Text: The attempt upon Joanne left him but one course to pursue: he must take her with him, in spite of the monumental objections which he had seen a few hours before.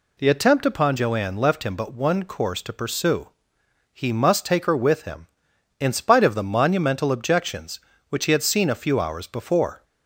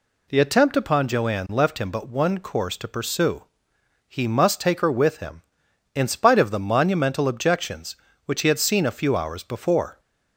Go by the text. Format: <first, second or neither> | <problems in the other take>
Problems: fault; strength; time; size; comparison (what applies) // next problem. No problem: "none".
neither | none